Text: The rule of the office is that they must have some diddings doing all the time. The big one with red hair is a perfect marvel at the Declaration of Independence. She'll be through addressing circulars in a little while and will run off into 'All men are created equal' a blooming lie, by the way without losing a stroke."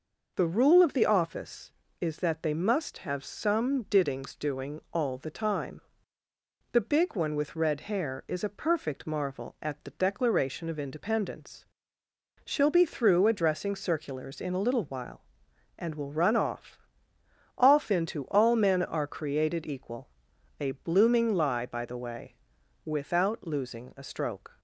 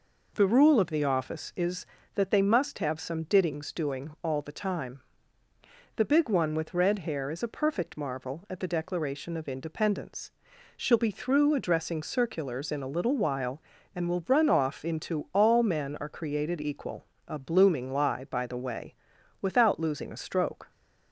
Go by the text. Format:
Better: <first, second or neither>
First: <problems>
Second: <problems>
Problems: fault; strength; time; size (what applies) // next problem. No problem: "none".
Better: second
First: says "off" twice; at 17.5 s // pauses between "equal" and "a"; noticeable; at 20.0 s; 0.52 s long // pauses between "way" and "without"; noticeable; at 22.3 s; 0.50 s long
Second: pauses between "equal" and "a"; slight; at 17.0 s; 0.24 s long // pauses between "way" and "without"; noticeable; at 18.9 s; 0.48 s long